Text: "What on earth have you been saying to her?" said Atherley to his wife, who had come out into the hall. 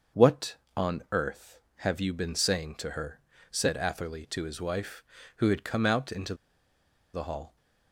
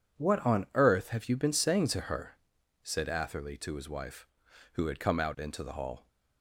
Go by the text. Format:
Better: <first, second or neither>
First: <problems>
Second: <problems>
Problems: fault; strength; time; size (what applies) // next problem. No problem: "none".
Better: second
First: starts louder than the rest; until 1.4 s; 6.5 dB // pauses between "into" and "the"; noticeable; at 6.3 s; 0.79 s long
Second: none